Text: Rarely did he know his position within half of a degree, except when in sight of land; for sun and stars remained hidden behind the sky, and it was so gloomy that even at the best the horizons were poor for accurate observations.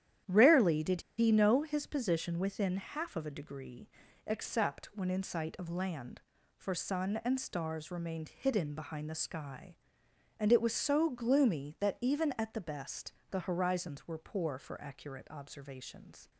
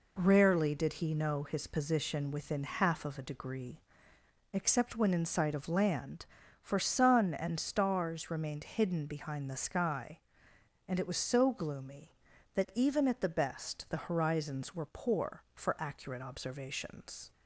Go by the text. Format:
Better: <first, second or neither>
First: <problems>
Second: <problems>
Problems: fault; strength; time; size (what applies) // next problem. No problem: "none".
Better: second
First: starts louder than the rest; strong; until 1.4 s; 11 dB // pauses between "did" and "he"; slight; at 1.0 s; 0.16 s long // pauses between "best" and "the"; slight; at 13.1 s; 0.16 s long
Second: none